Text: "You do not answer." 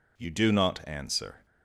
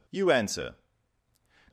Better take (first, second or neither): first